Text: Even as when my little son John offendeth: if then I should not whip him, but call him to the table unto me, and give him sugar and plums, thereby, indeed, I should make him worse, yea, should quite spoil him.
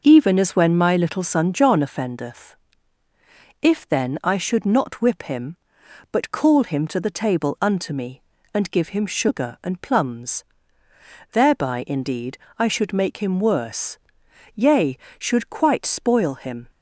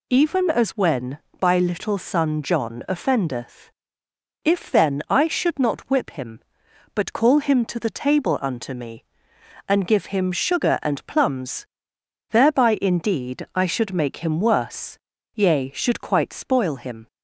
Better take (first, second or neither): first